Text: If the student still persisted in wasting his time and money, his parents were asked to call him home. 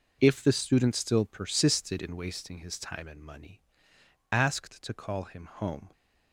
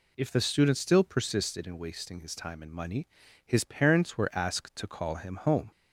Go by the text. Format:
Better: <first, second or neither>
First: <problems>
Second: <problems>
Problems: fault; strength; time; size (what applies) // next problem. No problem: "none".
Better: second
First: skips "his parents were"; at 3.9 s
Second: none